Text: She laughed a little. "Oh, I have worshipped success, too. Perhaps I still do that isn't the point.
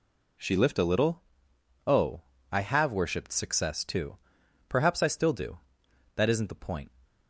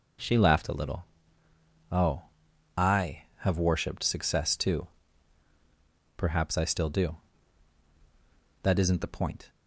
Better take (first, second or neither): second